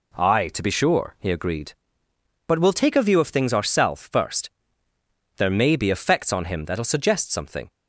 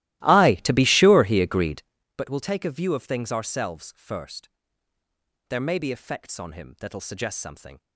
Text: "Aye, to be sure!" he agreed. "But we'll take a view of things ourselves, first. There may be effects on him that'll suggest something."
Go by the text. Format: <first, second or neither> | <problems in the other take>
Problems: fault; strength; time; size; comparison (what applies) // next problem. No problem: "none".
first | starts louder than the rest; strong; until 2.1 s; 16.5 dB